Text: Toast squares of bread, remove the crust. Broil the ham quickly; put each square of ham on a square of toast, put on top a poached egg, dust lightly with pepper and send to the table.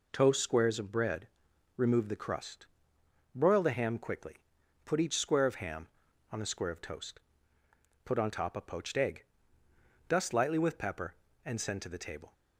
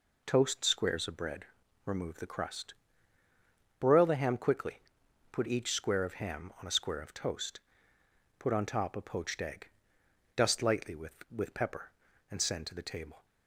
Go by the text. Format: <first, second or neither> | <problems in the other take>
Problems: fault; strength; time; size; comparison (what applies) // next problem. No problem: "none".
first | says "with" twice; at 11.2 s